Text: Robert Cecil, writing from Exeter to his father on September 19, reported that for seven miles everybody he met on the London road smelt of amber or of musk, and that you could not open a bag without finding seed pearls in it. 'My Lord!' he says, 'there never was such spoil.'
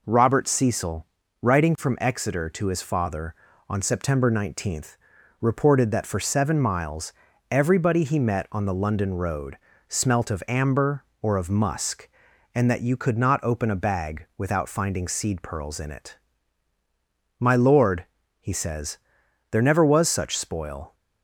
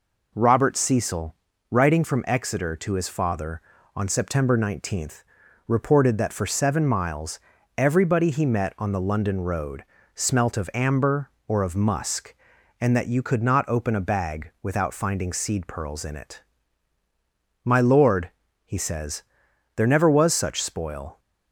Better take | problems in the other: neither | pauses between "miles" and "everybody"; the same in both // pauses between "road" and "smelt"; slight; the same in both

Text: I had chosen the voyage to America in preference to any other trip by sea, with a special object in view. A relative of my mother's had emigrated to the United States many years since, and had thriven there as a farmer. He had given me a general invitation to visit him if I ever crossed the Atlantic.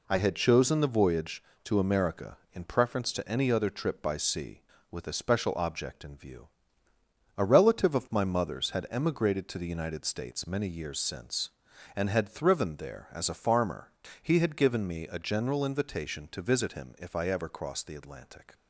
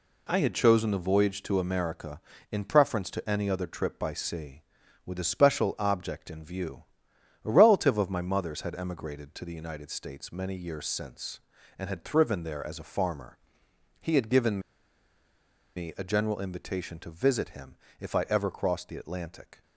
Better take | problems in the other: first | pauses between "given" and "me"; at 14.5 s; 1.1 s long // pauses between "him" and "if"; slight; at 17.7 s; 0.26 s long

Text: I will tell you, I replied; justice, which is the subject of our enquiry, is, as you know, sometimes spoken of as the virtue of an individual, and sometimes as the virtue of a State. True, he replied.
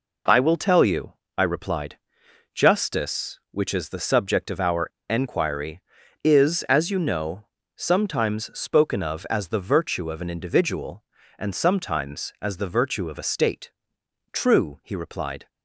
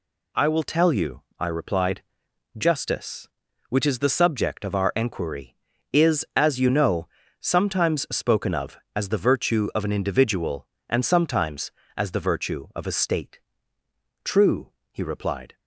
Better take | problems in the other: second | pauses between "our" and "enquiry"; slight; at 4.8 s; 0.19 s long

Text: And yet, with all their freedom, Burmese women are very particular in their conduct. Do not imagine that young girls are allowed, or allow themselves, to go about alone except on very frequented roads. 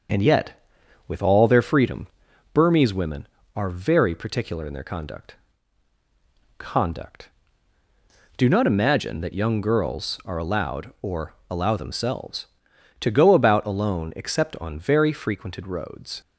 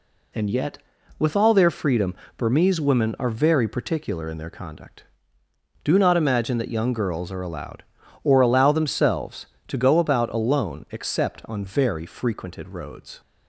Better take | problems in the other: second | starts louder than the rest; until 1.5 s; 6.5 dB // says "conduct" twice; at 6.5 s // pauses between "or" and "allow"; slight; at 11.3 s; 0.16 s long

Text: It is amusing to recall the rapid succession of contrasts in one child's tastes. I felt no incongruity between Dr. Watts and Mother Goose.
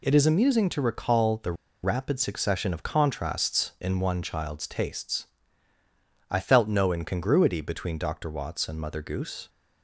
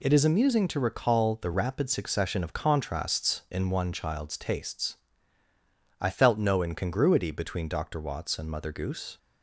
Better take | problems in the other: second | pauses between "the" and "rapid"; slight; at 1.5 s; 0.30 s long

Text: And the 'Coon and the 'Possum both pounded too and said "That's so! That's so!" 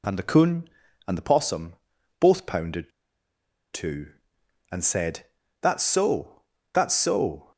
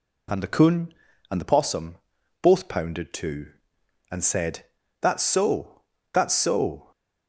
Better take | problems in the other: second | pauses between "Possum" and "both"; at 1.7 s; 0.42 s long; also in the second // pauses between "pounded" and "too"; noticeable; at 2.9 s; 0.82 s long // pauses between "said" and "That's"; slight; at 5.2 s; 0.36 s long; slight in the second

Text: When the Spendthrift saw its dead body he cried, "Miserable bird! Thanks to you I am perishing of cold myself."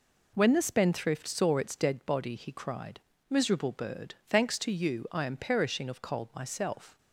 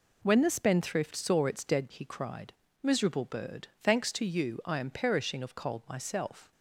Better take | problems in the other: first | skips "body"; at 1.9 s

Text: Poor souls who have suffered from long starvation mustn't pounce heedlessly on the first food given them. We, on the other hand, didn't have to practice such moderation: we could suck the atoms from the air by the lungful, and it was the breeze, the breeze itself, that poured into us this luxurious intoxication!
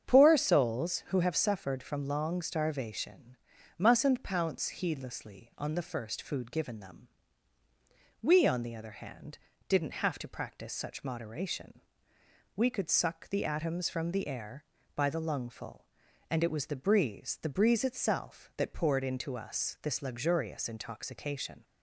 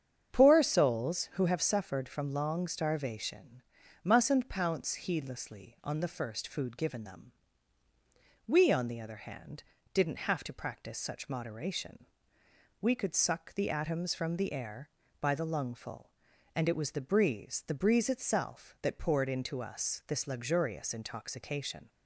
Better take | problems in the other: neither | starts louder than the rest; strong; the same in both // pauses between "starvation" and "mustn't"; the same in both

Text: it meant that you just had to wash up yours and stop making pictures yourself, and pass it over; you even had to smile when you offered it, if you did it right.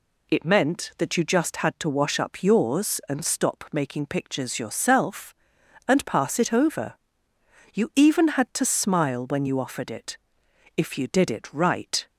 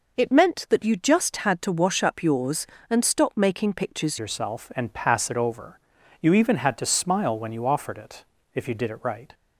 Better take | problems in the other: first | changes voice at "yourself"; from 4.1 s on; 5.2 s long

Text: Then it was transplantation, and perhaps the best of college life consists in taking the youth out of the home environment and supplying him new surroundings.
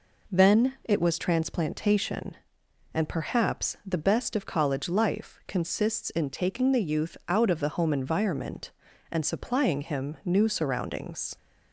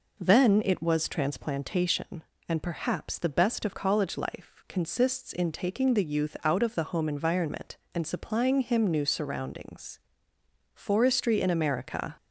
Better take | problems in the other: first | goes on to say "Forestry in America"; from 10.7 s on; 1.4 s long

